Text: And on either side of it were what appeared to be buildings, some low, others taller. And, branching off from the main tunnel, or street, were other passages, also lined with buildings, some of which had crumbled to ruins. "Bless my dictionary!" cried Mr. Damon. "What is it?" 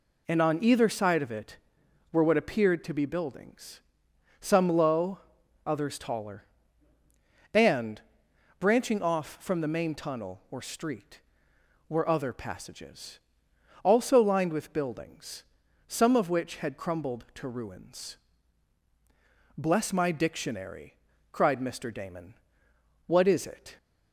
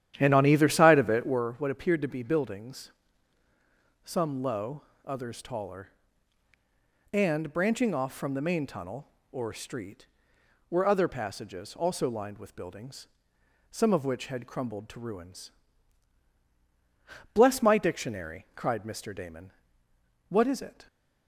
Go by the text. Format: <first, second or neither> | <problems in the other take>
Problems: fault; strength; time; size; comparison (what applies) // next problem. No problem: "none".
first | starts louder than the rest; strong; until 1.5 s; 11 dB